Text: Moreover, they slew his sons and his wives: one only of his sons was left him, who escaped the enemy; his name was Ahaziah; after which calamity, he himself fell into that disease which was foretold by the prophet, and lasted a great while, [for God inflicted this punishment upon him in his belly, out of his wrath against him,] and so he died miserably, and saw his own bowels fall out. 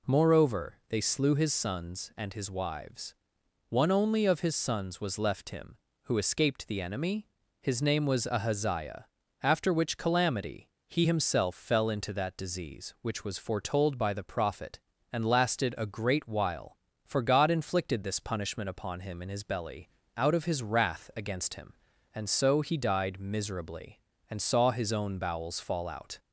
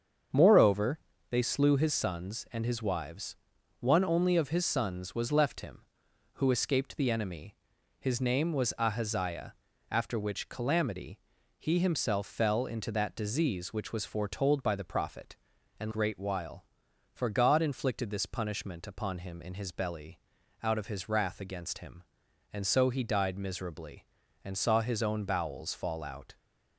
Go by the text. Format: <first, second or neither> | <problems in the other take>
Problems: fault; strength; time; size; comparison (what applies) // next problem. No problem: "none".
first | starts louder than the rest; until 1.6 s; 7 dB // skips "lasted a"; at 15.9 s